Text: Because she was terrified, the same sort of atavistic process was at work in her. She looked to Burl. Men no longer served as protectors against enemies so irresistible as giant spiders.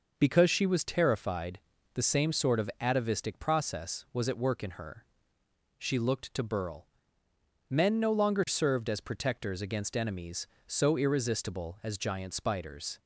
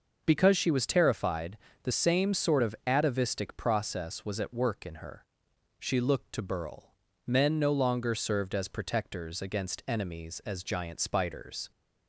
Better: first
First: none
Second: skips "so irresistible"; at 10.4 s

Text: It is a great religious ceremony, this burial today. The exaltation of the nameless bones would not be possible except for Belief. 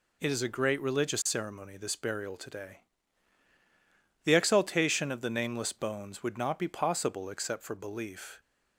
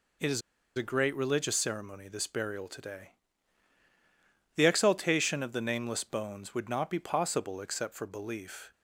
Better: first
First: none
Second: pauses between "is" and "a"; slight; at 0.4 s; 0.35 s long

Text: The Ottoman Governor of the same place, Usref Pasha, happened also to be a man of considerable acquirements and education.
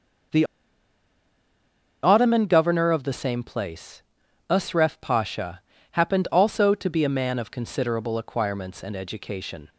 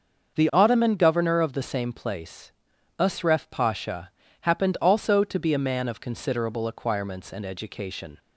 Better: second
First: starts louder than the rest; until 2.9 s; 6.5 dB // pauses between "The" and "Ottoman"; strong; at 0.4 s; 1.5 s long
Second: starts louder than the rest; until 1.3 s; 6.5 dB

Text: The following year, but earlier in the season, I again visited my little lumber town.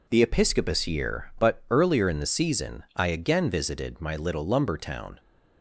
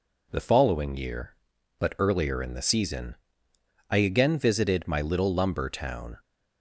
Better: second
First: says "episcopus" for "following"; at 0.2 s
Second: none

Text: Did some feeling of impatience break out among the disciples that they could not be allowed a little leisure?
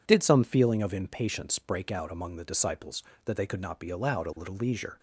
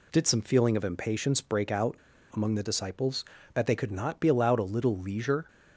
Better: first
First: none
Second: pauses between "out" and "among"; at 1.9 s; 0.37 s long

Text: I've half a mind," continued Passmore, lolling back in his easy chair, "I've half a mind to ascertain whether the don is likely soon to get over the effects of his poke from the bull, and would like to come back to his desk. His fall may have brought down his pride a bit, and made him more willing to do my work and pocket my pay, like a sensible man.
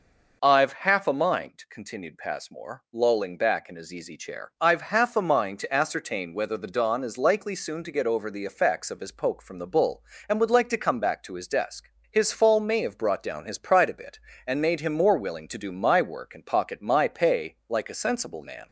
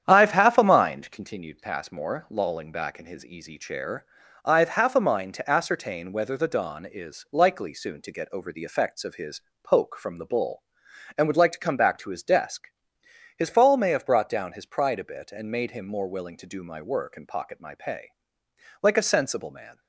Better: first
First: none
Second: starts louder than the rest; strong; until 1.3 s; 9 dB // pauses between "his" and "poke"; slight; at 9.3 s; 0.24 s long

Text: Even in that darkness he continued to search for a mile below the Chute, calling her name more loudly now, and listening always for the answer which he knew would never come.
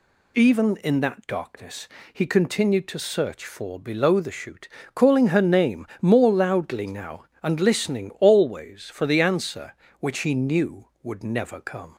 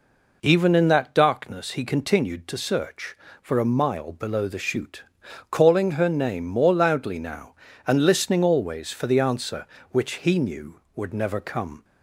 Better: second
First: pauses between "darkness" and "he"; slight; at 1.8 s; 0.24 s long // skips "a mile"; at 3.7 s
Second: none

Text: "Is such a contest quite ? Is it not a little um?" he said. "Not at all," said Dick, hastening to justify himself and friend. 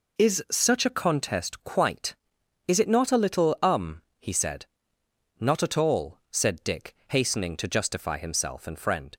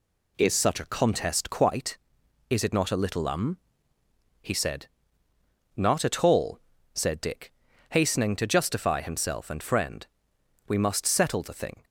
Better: first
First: none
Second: goes on to say "We must settle the thing"; noticeable; from 10.6 s on; 1.1 s long

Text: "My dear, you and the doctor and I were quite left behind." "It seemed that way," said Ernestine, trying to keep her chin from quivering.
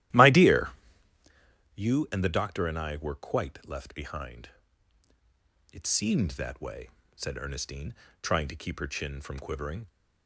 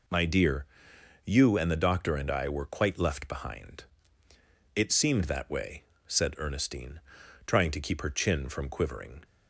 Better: second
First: starts louder than the rest; strong; until 1.3 s; 14 dB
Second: none

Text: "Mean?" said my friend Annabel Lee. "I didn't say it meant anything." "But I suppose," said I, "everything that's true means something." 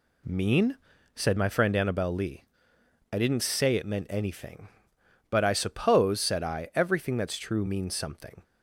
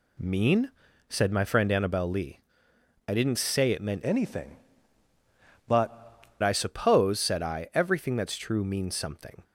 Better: first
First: none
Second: changes voice from "anything" to "But"; from 4.0 to 6.2 s; 2.2 s long

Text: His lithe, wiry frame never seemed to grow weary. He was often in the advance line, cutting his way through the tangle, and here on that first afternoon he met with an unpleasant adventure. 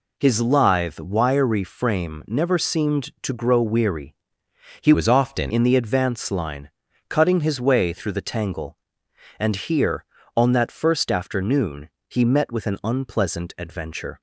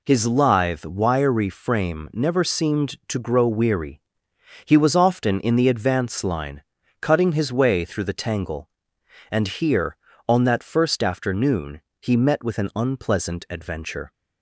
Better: second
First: changes voice from "was" to "often"; from 4.9 to 5.5 s; 0.6 s long // pauses between "afternoon" and "he"; slight; at 11.8 s; 0.18 s long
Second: pauses between "afternoon" and "he"; slight; at 11.8 s; 0.18 s long

